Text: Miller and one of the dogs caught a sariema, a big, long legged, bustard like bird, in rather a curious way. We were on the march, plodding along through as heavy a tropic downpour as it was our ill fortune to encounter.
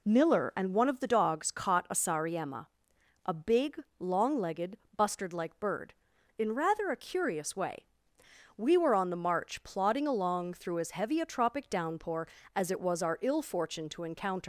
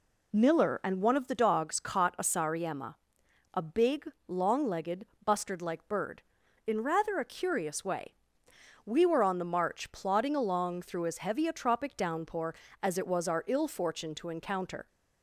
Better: second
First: leaves "encounter" unfinished; at 14.4 s; 135 ms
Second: none

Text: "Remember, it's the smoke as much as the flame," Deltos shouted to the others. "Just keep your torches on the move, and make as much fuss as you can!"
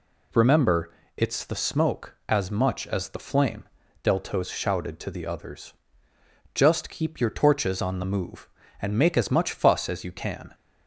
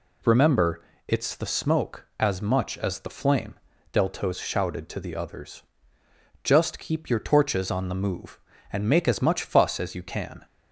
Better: neither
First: none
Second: none

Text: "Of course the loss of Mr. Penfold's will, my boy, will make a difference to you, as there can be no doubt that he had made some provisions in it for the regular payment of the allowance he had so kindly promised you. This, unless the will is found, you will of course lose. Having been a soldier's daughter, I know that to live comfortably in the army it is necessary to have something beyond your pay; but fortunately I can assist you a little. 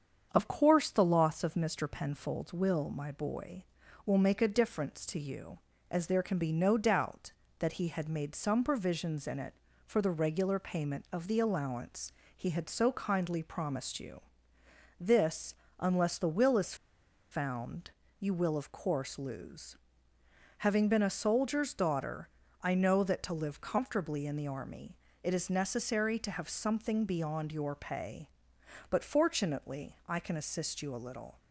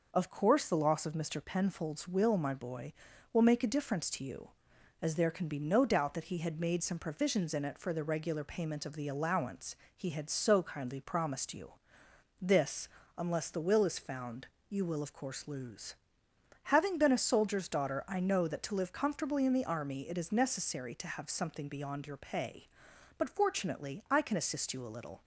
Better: second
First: starts louder than the rest; strong; until 1.3 s; 7.5 dB // pauses between "allowance" and "he"; slight; at 12.1 s; 0.24 s long // pauses between "is" and "found"; noticeable; at 16.7 s; 0.57 s long // pauses between "army" and "it"; slight; at 24.9 s; 0.24 s long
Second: pauses between "allowance" and "he"; slight; at 9.7 s; 0.22 s long

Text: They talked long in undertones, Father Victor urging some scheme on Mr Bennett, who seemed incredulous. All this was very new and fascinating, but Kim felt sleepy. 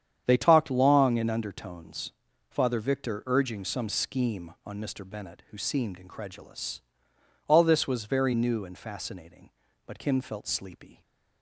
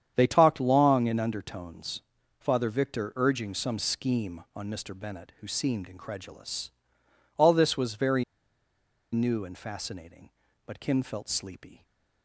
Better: first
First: starts louder than the rest; strong; until 1.2 s; 8.5 dB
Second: starts louder than the rest; strong; until 1.1 s; 8.5 dB // pauses between "very" and "new"; noticeable; at 8.2 s; 0.89 s long

